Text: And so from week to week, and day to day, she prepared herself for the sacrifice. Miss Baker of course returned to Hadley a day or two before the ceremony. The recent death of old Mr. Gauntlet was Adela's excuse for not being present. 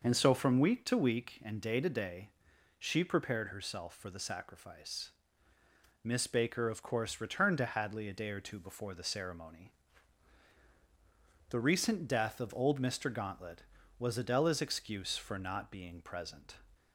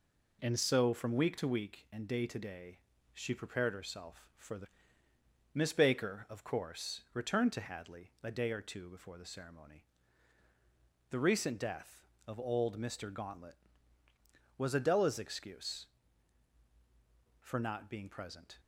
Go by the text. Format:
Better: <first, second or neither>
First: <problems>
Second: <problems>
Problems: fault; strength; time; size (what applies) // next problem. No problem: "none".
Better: first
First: none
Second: skips "sacrifice"; at 5.0 s